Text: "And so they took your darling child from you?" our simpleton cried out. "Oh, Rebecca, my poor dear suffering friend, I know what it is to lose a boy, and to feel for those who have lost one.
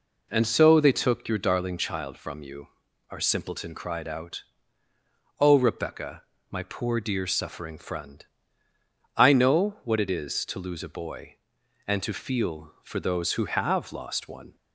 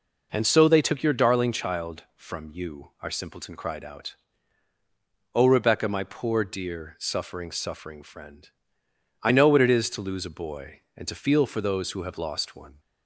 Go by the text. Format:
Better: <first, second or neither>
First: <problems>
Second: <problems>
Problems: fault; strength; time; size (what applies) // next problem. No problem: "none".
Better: first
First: none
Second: says "suffering" twice; at 7.5 s